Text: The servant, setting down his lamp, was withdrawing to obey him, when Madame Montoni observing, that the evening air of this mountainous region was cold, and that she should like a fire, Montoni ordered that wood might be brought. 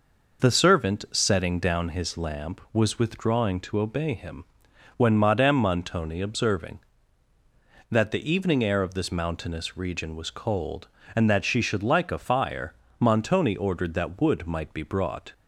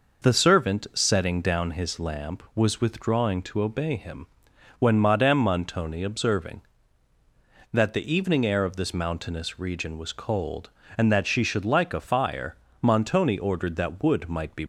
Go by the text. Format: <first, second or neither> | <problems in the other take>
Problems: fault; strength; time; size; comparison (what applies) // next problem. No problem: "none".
first | stops before "brought"; at 14.6 s